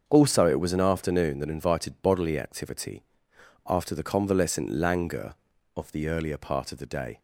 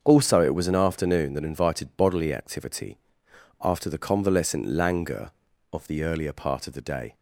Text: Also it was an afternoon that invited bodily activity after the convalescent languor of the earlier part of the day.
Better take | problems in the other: neither | starts louder than the rest; the same in both // pauses between "activity" and "after"; noticeable; the same in both

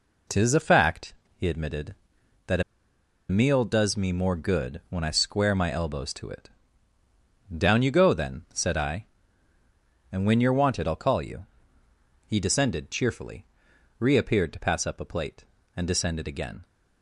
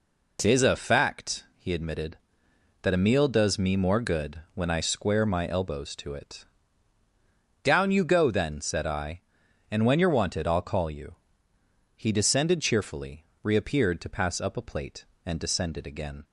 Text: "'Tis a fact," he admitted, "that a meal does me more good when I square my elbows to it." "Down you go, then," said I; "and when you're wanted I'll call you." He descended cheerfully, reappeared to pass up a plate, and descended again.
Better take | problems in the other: second | pauses between "a" and "meal"; noticeable; at 2.6 s; 0.68 s long

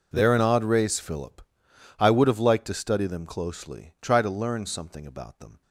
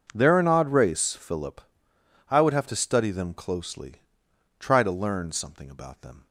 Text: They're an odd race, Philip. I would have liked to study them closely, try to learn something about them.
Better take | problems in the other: first | skips "liked"; at 2.6 s

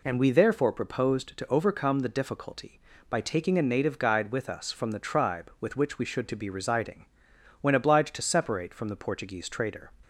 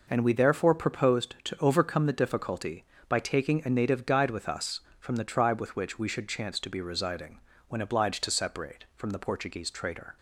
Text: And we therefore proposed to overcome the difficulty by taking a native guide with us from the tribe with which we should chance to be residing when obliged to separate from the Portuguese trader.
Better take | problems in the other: second | skips "chance"; at 6.2 s // pauses between "residing" and "when"; noticeable; at 7.0 s; 0.54 s long; slight in the second

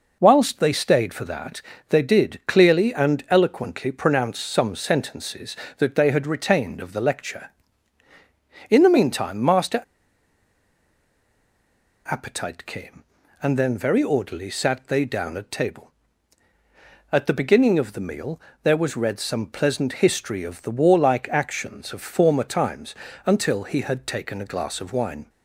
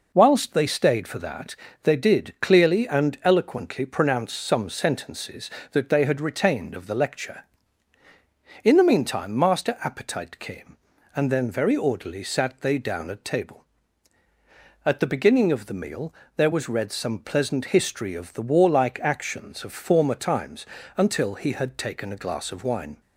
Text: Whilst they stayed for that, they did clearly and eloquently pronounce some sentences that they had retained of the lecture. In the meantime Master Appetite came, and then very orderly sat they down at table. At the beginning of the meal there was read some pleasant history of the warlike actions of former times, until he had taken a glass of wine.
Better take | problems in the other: second | pauses between "Master" and "Appetite"; strong; at 9.8 s; 2.2 s long // pauses between "meal" and "there"; slight; at 18.3 s; 0.24 s long; slight in the second

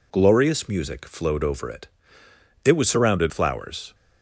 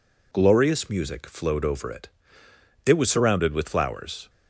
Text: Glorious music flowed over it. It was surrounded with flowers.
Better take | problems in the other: second | skips "with"; at 3.3 s

